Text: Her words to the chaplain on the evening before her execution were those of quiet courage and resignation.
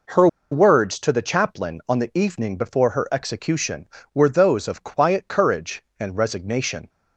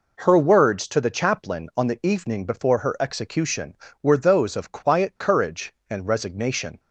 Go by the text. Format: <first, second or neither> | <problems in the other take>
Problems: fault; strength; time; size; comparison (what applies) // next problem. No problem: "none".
second | pauses between "Her" and "words"; slight; at 0.2 s; 0.24 s long